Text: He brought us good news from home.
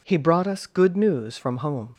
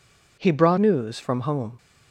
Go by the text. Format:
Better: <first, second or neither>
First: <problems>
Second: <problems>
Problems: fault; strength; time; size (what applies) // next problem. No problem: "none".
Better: first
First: none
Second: skips "us good"; at 0.7 s